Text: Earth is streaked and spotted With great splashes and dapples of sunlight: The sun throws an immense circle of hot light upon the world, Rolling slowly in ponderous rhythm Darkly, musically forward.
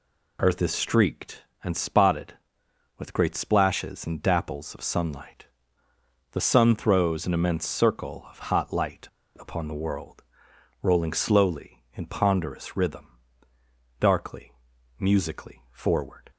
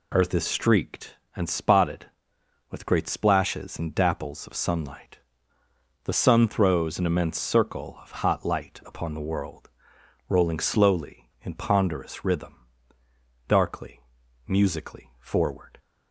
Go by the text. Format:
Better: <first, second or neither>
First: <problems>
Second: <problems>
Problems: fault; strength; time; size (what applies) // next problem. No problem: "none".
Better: second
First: pauses between "light" and "upon"; slight; at 9.0 s; 0.32 s long // pauses between "rhythm" and "Darkly"; noticeable; at 13.1 s; 0.82 s long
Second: pauses between "rhythm" and "Darkly"; noticeable; at 12.6 s; 0.82 s long